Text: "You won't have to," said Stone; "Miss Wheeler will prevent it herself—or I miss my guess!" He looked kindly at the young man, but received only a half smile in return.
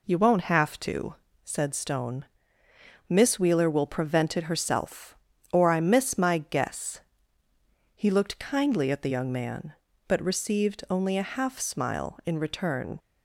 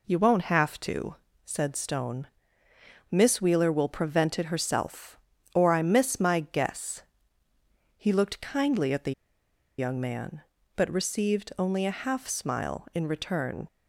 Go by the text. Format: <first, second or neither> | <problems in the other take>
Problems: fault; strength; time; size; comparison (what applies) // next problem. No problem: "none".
first | pauses between "the" and "young"; noticeable; at 9.1 s; 0.66 s long